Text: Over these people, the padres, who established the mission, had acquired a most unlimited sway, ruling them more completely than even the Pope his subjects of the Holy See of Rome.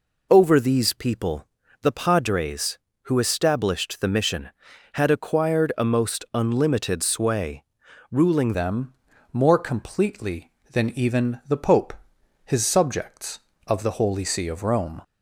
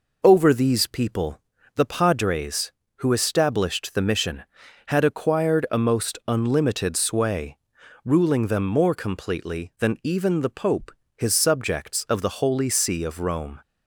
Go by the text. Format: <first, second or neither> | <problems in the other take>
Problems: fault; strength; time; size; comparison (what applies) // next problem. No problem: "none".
second | changes voice at "them"; from 8.5 s on; 6.5 s long // pauses between "them" and "more"; at 8.9 s; 0.40 s long // pauses between "Pope" and "his"; noticeable; at 11.9 s; 0.50 s long; slight in the second